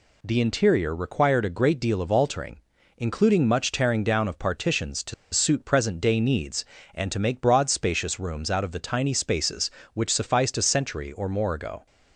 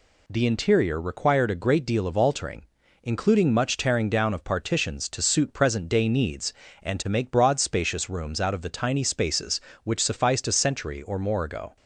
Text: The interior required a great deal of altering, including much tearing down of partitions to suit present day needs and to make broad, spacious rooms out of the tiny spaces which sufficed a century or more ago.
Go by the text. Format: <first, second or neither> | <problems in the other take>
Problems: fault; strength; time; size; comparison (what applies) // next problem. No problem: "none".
second | pauses between "to" and "suit"; slight; at 5.1 s; 0.19 s long